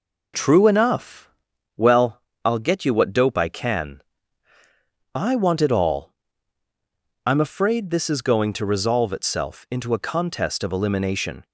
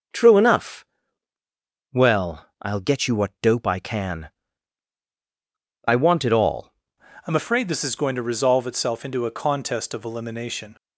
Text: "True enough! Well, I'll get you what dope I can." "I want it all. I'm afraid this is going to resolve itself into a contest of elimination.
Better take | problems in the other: first | starts louder than the rest; until 2.2 s; 6.5 dB // changes voice at "I'm"; from 7.2 s on; 3.5 s long

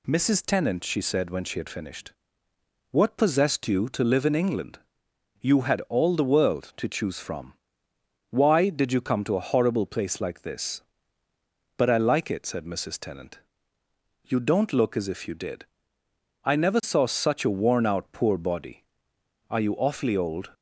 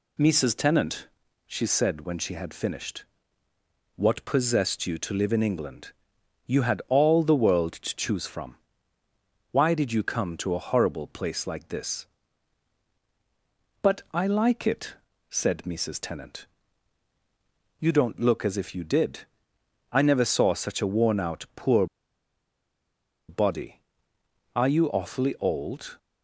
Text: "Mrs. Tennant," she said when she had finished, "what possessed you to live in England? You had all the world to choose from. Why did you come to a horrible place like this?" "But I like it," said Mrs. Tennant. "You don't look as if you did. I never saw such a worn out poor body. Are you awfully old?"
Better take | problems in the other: first | pauses between "poor" and "body"; strong; at 21.8 s; 1.4 s long

